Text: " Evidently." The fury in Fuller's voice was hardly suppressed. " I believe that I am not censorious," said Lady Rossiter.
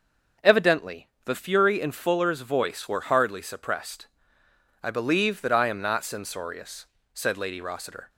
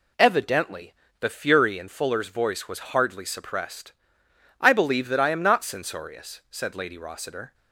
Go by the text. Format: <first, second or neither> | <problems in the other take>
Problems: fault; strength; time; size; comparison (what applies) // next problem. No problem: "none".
second | starts louder than the rest; until 1.5 s; 6.5 dB // says "were" for "was"; at 2.8 s